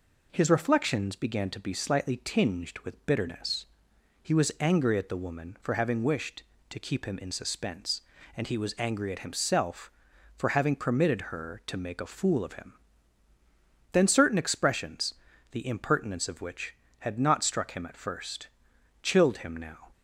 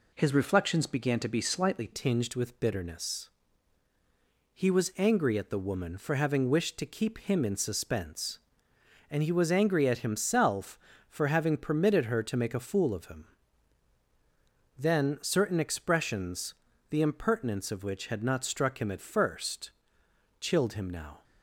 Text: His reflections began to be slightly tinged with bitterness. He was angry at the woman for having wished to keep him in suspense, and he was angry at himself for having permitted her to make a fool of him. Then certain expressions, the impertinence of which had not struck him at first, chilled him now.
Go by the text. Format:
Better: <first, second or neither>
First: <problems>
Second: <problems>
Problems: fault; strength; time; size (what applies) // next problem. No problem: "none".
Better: first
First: none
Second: changes voice at "tinged"; from 1.9 s on; 19.3 s long